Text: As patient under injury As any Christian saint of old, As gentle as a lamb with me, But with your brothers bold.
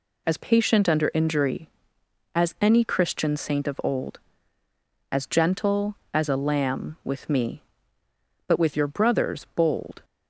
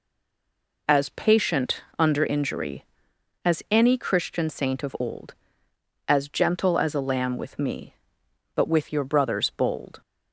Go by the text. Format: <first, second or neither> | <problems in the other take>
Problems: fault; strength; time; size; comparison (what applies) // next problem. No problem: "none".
first | stays silent before the first word; slight; until 0.8 s; 0.8 s long